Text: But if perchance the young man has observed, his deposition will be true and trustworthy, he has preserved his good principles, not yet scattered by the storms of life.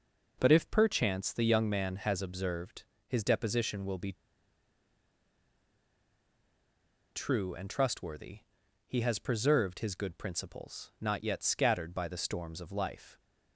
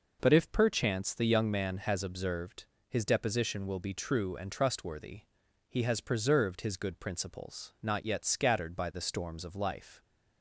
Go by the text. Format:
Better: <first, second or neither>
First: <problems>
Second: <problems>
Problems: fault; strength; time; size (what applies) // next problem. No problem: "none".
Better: second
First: pauses between "be" and "true"; strong; at 4.1 s; 3.0 s long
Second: none